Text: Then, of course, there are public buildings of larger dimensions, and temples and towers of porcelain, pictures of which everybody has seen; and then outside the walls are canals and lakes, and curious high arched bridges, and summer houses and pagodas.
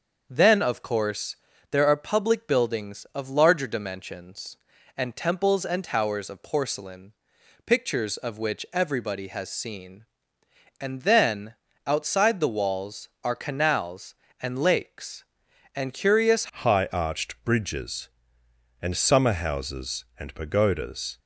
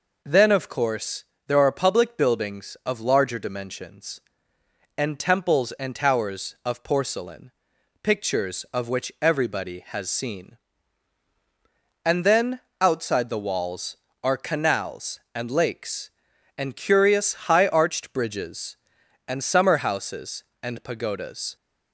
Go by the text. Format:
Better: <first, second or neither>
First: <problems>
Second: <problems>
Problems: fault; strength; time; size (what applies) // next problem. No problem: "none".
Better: second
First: starts louder than the rest; until 1.3 s; 6.5 dB // pauses between "then" and "outside"; slight; at 11.5 s; 0.32 s long // changes voice at "high"; from 16.4 s on; 4.7 s long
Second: pauses between "then" and "outside"; slight; at 12.5 s; 0.22 s long